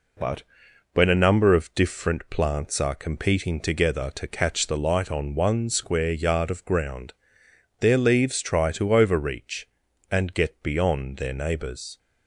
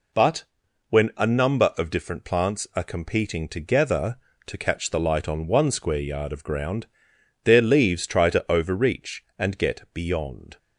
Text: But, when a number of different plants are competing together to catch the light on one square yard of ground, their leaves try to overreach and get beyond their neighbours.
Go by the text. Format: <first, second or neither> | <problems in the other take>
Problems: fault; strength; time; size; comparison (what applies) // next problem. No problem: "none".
first | stops before "their neighbours"; at 10.5 s